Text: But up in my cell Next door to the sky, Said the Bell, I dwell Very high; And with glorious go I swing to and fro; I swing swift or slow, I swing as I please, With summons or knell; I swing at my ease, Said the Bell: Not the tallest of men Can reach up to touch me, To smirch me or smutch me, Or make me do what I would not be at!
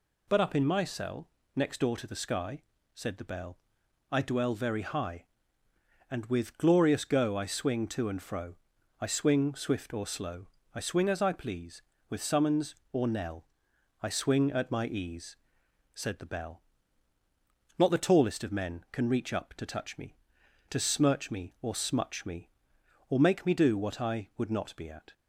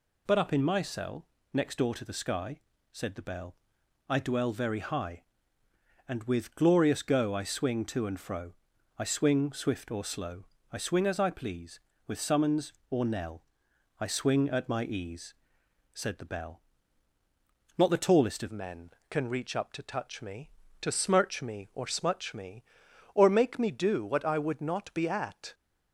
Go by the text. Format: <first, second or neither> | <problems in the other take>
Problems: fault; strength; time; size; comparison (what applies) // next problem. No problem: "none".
first | pauses between "cell" and "Next"; slight; at 1.2 s; 0.26 s long; slight in the first // changes voice at "men"; from 18.4 s on; 7.1 s long